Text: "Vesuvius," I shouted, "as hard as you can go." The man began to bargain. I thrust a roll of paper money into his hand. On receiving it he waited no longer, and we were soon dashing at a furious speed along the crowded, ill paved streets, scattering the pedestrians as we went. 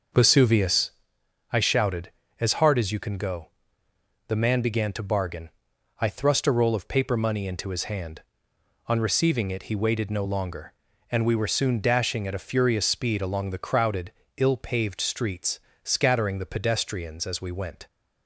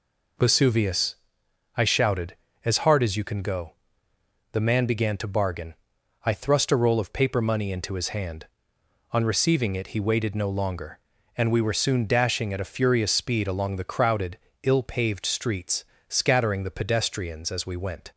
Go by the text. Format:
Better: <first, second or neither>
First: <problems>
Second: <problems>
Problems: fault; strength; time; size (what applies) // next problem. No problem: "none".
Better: second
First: starts louder than the rest; noticeable; until 1.1 s; 6 dB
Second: none